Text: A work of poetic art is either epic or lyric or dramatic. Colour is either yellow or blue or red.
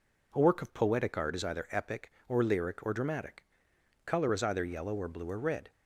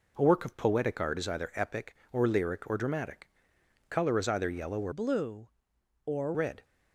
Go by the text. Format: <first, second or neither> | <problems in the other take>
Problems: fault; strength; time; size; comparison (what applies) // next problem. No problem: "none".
first | changes voice from "blue" to "or"; from 4.9 to 6.3 s; 1.4 s long